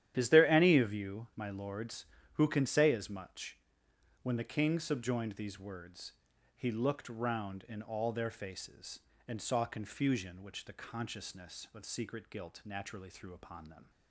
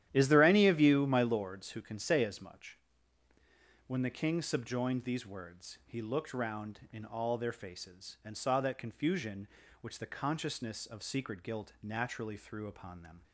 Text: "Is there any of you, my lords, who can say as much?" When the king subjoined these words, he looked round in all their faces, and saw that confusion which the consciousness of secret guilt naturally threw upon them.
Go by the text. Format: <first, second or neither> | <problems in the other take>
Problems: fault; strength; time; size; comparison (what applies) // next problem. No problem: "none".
second | starts louder than the rest; strong; until 1.1 s; 11.5 dB; strong in the second // skips "that"; at 9.6 s